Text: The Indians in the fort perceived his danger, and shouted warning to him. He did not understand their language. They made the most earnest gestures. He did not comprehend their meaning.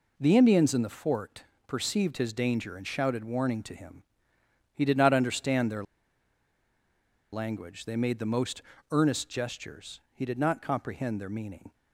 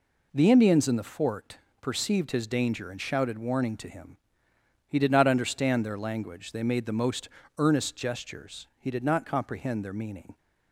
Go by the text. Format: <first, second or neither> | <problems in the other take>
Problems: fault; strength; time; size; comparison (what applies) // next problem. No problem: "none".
second | pauses between "fort" and "perceived"; slight; at 1.4 s; 0.24 s long; slight in the second // pauses between "their" and "language"; strong; at 5.8 s; 1.4 s long // pauses between "most" and "earnest"; slight; at 8.6 s; 0.30 s long; slight in the second